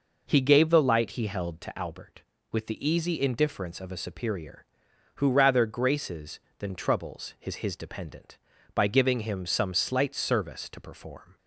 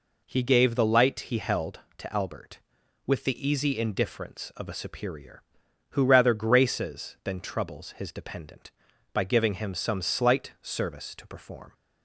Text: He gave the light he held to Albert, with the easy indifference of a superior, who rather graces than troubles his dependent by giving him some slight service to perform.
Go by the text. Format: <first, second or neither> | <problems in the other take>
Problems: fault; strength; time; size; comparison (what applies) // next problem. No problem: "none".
second | says "his" twice; at 7.5 s